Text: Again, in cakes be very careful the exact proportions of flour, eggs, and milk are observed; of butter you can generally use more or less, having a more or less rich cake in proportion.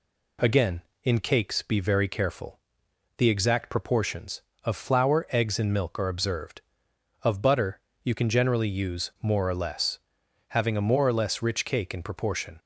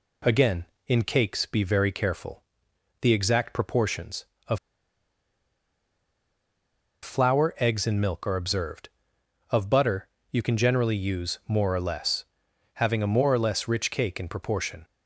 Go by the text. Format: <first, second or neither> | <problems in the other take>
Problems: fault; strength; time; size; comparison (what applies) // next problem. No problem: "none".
first | pauses between "careful" and "the"; noticeable; at 2.4 s; 0.58 s long; noticeable in the first // pauses between "of" and "flour"; strong; at 4.5 s; 2.4 s long // pauses between "butter" and "you"; slight; at 10.0 s; 0.22 s long; slight in the first